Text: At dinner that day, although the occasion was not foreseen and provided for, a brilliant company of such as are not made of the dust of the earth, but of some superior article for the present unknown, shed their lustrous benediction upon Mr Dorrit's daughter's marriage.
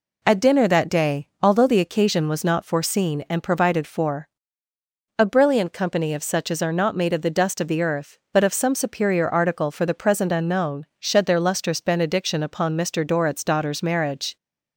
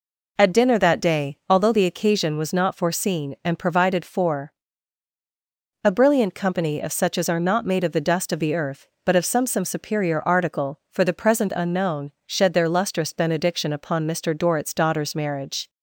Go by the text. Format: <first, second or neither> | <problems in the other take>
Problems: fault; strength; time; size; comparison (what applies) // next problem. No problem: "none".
first | says "some" twice; at 9.4 s